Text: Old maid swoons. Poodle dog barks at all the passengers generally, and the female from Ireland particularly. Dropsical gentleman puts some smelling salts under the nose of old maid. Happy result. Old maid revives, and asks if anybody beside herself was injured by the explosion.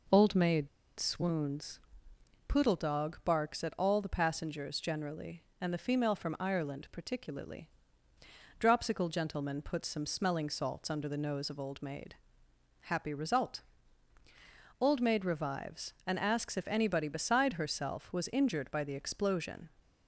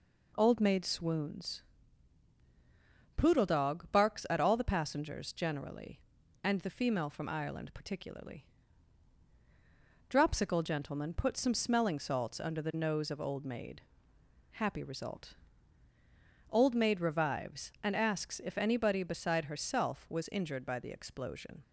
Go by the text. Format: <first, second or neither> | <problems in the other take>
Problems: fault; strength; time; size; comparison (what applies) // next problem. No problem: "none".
second | pauses between "maid" and "swoons"; slight; at 0.6 s; 0.31 s long